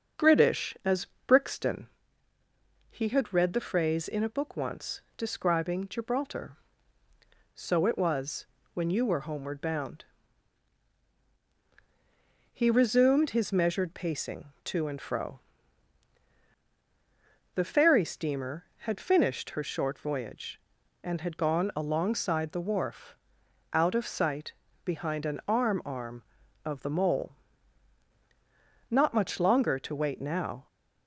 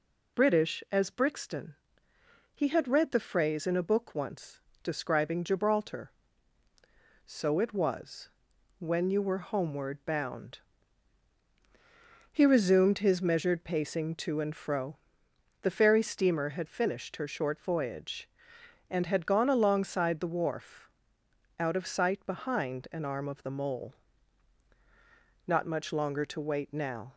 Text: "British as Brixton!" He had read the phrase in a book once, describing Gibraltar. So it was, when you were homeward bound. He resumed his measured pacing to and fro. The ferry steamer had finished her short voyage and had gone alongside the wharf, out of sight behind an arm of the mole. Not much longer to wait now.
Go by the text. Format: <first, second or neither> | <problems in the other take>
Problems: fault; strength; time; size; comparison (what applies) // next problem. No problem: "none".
second | starts louder than the rest; until 1.4 s; 6.5 dB // pauses between "as" and "Brixton"; slight; at 1.0 s; 0.22 s long // pauses between "sight" and "behind"; slight; at 24.5 s; 0.32 s long // says "arm" twice; at 25.8 s